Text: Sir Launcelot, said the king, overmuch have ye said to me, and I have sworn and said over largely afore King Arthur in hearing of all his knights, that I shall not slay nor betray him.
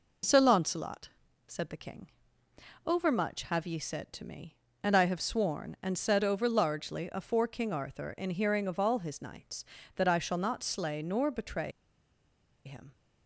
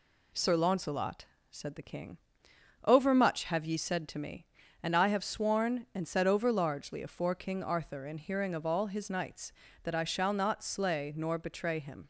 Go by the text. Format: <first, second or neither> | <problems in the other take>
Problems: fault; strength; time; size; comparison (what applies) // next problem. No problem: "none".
second | pauses between "betray" and "him"; noticeable; at 11.7 s; 0.94 s long